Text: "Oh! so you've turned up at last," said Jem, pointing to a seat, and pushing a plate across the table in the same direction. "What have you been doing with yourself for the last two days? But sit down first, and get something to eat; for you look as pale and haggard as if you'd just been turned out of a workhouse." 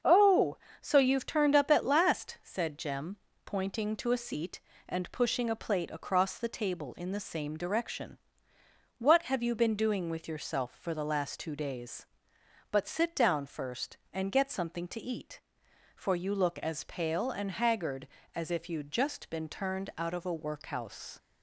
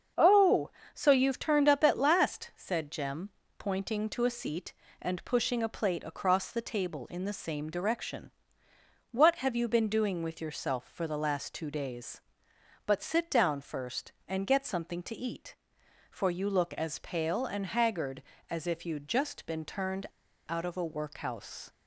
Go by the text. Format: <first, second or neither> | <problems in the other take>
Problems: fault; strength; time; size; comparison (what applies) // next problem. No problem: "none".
first | starts louder than the rest; until 1.4 s; 7 dB; also in the first // pauses between "turned" and "out"; at 20.0 s; 0.43 s long